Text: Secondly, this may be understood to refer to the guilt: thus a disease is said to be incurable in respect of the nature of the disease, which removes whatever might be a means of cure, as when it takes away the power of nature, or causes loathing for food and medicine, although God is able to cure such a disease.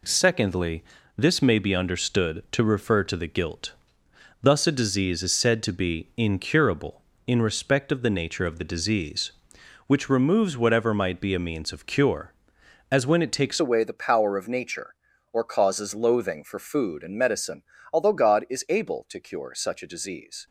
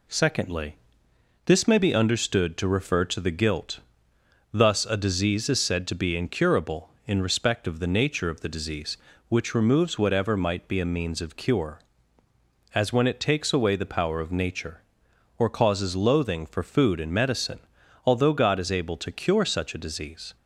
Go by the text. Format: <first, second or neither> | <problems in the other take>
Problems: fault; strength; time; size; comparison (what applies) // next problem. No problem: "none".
second | changes voice at "away"; from 13.5 s on; 6.9 s long